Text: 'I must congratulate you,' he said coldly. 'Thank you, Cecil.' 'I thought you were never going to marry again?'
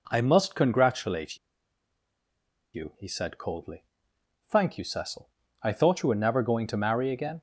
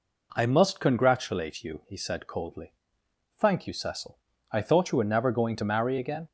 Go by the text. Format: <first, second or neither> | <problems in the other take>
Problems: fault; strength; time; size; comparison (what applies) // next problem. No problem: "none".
second | pauses between "congratulate" and "you"; strong; at 1.3 s; 1.3 s long